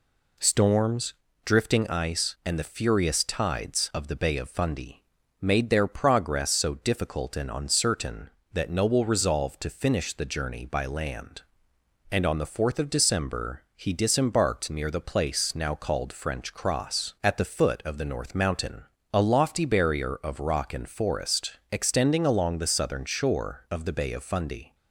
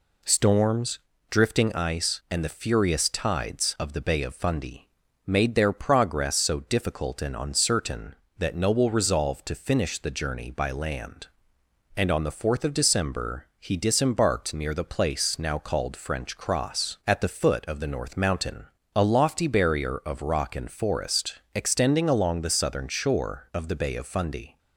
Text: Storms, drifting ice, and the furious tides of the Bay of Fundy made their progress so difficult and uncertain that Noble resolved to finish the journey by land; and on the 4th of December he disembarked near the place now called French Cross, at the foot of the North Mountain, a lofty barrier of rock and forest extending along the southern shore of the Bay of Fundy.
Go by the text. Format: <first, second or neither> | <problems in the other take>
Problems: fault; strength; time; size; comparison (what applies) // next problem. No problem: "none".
neither | pauses between "Fundy" and "made"; the same in both // pauses between "forest" and "extending"; slight; the same in both